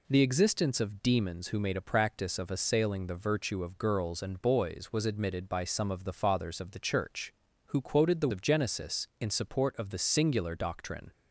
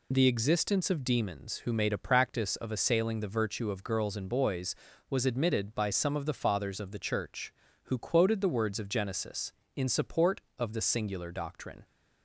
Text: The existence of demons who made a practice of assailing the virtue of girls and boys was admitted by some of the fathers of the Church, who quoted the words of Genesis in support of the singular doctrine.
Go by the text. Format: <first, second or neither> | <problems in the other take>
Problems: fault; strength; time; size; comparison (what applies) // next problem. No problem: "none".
second | skips "words"; at 8.3 s